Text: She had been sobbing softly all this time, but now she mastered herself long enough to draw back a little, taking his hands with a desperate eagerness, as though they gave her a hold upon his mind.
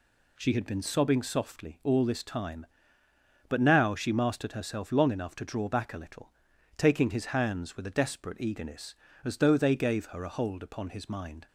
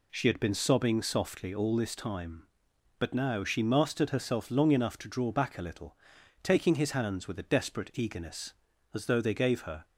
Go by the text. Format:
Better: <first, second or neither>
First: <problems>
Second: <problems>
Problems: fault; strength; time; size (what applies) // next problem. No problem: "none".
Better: first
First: none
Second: stops before "a hold upon his mind"; at 9.8 s